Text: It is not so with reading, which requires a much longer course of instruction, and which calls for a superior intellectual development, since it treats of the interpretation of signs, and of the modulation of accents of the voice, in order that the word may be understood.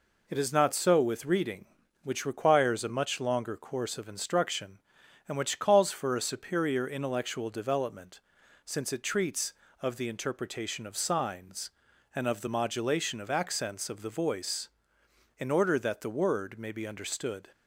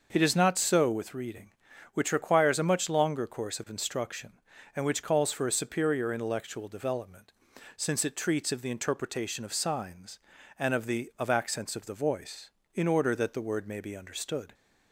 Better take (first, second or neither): first